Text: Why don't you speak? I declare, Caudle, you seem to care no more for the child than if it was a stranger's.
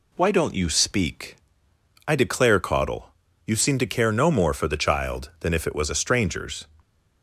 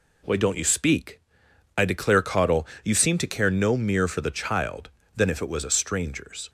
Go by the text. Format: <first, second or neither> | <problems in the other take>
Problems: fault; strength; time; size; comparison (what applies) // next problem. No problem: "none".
first | says "mere" for "more"; at 3.7 s